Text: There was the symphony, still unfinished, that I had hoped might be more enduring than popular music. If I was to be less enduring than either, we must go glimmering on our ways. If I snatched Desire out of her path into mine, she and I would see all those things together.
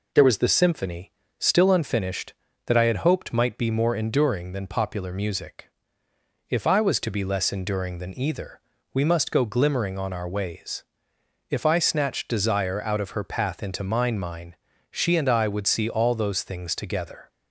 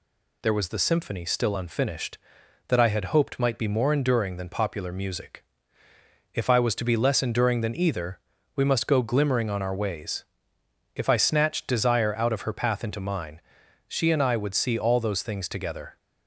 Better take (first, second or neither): second